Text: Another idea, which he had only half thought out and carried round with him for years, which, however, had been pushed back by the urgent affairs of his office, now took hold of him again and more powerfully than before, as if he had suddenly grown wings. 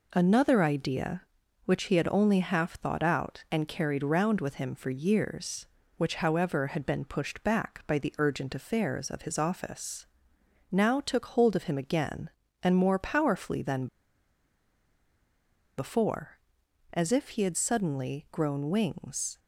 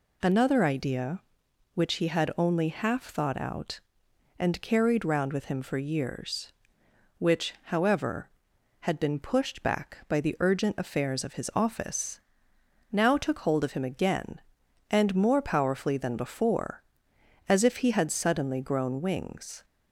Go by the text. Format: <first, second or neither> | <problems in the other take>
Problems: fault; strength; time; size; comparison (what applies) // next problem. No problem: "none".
second | pauses between "than" and "before"; strong; at 13.8 s; 1.9 s long